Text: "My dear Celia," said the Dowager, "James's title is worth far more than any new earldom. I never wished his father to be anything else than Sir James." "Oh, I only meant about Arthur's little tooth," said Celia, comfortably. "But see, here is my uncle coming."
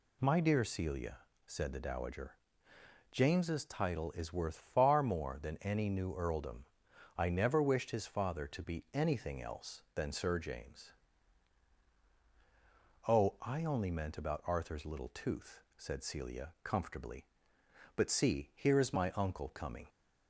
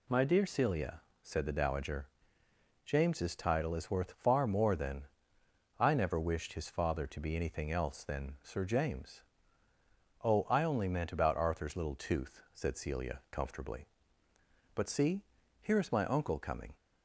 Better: first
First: none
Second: skips "any new earldom"; at 5.4 s

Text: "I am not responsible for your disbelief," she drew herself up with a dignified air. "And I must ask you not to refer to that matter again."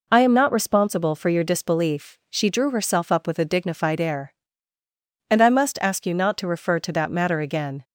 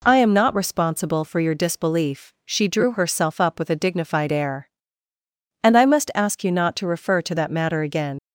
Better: first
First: none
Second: leaves "again" unfinished; at 8.1 s; 65 ms

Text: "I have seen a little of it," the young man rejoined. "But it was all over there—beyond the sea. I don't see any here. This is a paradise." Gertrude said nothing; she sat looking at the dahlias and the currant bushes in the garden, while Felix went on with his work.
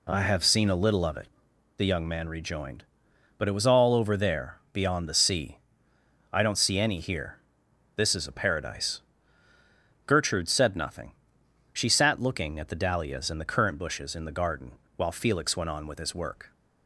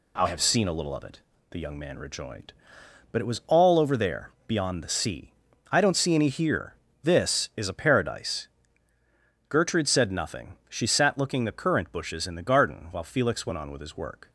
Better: first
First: none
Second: skips "at the dahlias and"; at 11.4 s

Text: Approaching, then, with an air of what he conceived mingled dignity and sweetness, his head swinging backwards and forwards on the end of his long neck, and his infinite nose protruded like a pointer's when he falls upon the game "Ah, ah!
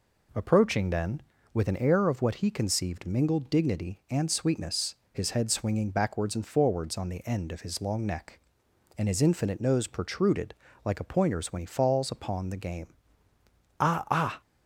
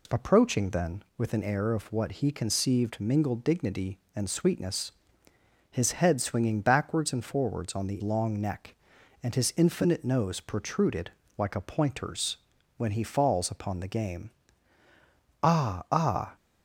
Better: first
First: pauses between "protruded" and "like"; slight; at 10.5 s; 0.30 s long // pauses between "game" and "Ah"; noticeable; at 12.9 s; 0.88 s long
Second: skips "end of his"; at 8.0 s // pauses between "protruded" and "like"; slight; at 11.0 s; 0.28 s long // pauses between "pointer's" and "when"; at 12.3 s; 0.40 s long // pauses between "game" and "Ah"; at 14.2 s; 1.1 s long

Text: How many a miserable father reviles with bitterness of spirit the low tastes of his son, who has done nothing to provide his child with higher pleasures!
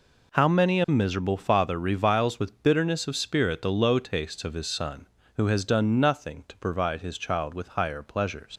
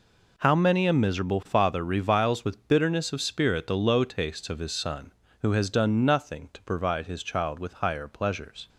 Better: second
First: leaves "pleasures" unfinished; at 8.5 s; 70 ms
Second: none

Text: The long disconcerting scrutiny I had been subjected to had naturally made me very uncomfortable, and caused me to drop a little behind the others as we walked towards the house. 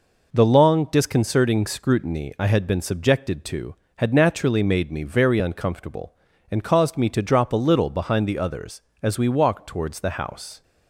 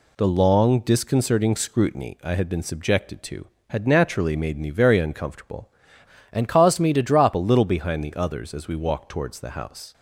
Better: first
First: none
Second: changes voice from "and" to "drop"; from 6.3 to 7.3 s; 1.0 s long

